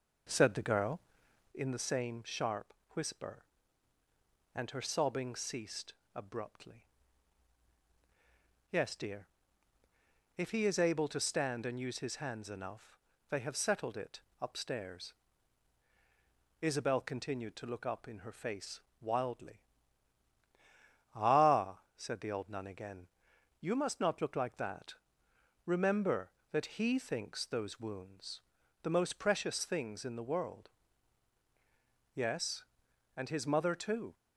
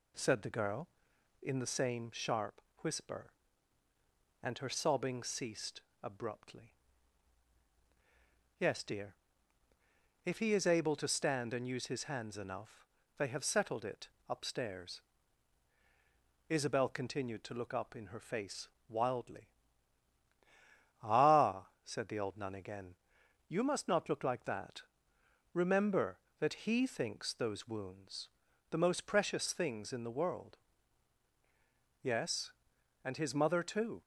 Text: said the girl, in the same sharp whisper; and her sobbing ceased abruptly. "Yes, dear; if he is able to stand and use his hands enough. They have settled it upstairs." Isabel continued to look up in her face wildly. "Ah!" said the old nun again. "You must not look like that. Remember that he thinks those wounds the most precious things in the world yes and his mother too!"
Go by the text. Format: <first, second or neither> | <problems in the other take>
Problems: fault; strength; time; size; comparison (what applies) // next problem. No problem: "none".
second | starts louder than the rest; noticeable; until 1.6 s; 5.5 dB // pauses between "sharp" and "whisper"; slight; at 2.7 s; 0.18 s long; slight in the second // pauses between "ceased" and "abruptly"; slight; at 5.9 s; 0.20 s long; slight in the second // pauses between "it" and "upstairs"; slight; at 14.2 s; 0.18 s long; slight in the second // pauses between "face" and "wildly"; slight; at 18.7 s; 0.22 s long; slight in the second // pauses between "wounds" and "the"; at 28.3 s; 0.42 s long; also in the second // pauses between "world" and "yes"; strong; at 30.6 s; 1.4 s long; strong in the second